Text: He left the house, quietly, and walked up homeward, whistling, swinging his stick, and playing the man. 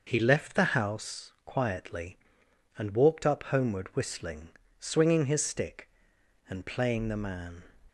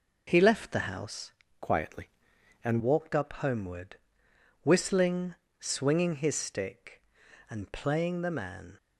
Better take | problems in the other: first | changes voice from "quietly" to "and"; from 1.6 to 2.8 s; 1.2 s long

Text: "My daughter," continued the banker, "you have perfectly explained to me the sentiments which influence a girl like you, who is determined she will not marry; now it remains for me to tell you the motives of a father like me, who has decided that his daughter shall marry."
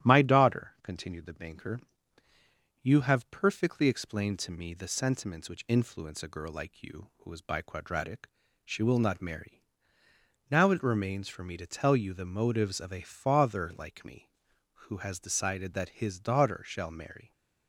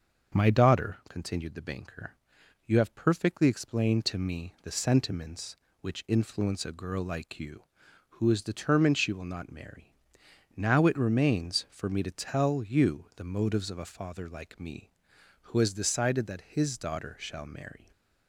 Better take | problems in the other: second | starts louder than the rest; strong; until 1.1 s; 12 dB; also in the second // says "biquadratic" for "determined"; at 7.4 s

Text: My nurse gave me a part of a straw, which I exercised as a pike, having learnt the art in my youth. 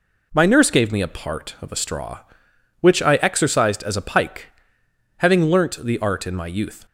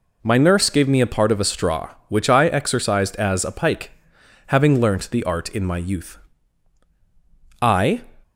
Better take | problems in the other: first | goes on to say "I"; slight; from 7.6 s on; 0.40 s long

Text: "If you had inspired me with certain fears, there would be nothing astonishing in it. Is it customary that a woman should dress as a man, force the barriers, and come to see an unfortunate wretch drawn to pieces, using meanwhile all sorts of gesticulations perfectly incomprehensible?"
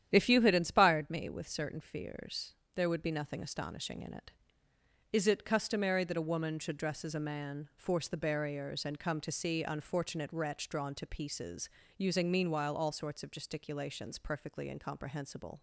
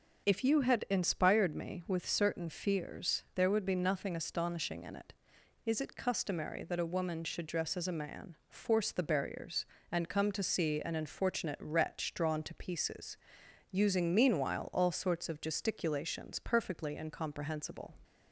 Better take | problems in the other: second | starts louder than the rest; strong; until 1.1 s; 10 dB; also in the second // skips "an"; at 9.6 s

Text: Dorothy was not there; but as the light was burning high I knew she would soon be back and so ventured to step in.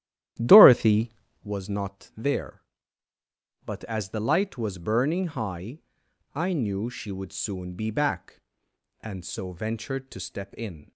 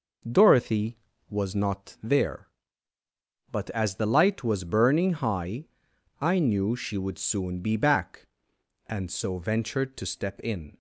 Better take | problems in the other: second | starts louder than the rest; strong; until 1.5 s; 12 dB // pauses between "high" and "I"; noticeable; at 5.7 s; 0.54 s long; noticeable in the second

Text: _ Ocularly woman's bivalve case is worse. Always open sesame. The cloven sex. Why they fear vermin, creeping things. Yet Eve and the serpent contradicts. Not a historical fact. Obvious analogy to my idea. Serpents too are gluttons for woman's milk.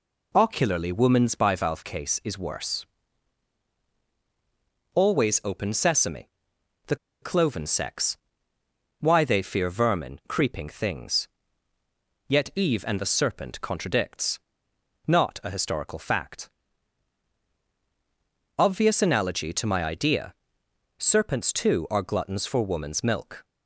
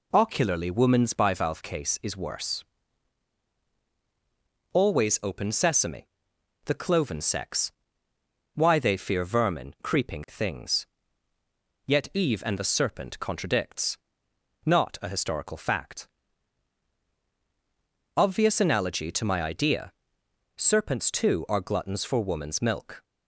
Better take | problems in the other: second | pauses between "The" and "cloven"; slight; at 6.9 s; 0.26 s long

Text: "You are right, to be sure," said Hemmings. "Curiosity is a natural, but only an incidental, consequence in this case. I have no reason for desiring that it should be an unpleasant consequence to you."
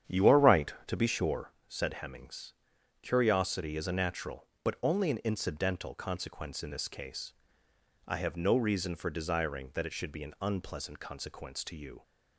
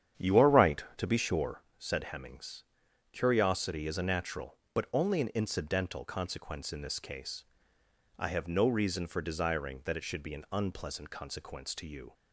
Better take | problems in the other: neither | starts louder than the rest; strong; the same in both

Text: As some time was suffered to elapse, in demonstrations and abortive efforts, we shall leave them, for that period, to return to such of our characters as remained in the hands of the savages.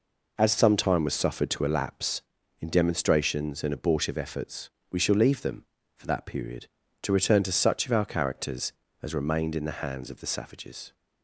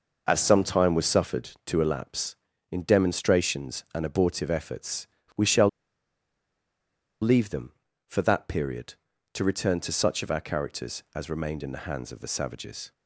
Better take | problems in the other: first | pauses between "shall" and "leave"; strong; at 5.6 s; 1.5 s long

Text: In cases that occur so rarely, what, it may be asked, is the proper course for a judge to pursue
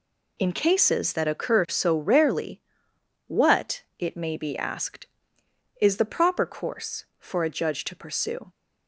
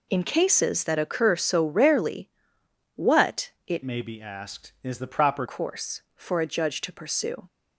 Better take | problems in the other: first | changes voice from "may" to "proper"; from 3.8 to 5.4 s; 1.6 s long

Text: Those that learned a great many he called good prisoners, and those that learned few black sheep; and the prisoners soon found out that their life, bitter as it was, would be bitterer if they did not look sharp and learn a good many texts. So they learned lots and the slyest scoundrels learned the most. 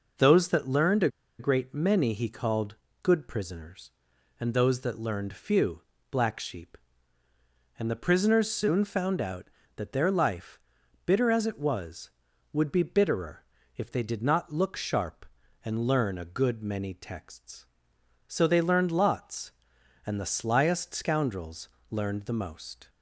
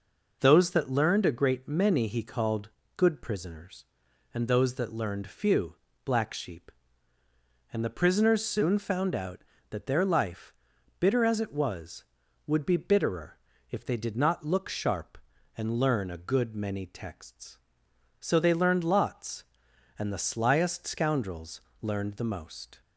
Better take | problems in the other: second | pauses between "a" and "great"; slight; at 1.0 s; 0.30 s long // pauses between "called" and "good"; slight; at 2.7 s; 0.26 s long; slight in the second // pauses between "few" and "black"; slight; at 5.8 s; 0.28 s long; slight in the second // pauses between "bitterer" and "if"; slight; at 13.4 s; 0.32 s long; slight in the second // pauses between "scoundrels" and "learned"; slight; at 21.6 s; 0.20 s long; slight in the second

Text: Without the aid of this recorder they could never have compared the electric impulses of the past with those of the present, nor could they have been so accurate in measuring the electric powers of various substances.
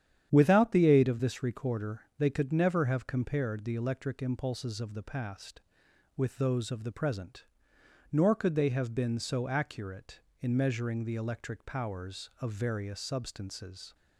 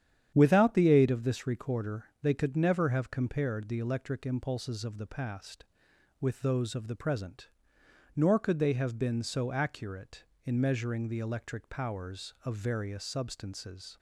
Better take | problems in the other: neither | starts louder than the rest; strong; the same in both // pauses between "recorder" and "they"; slight; the same in both

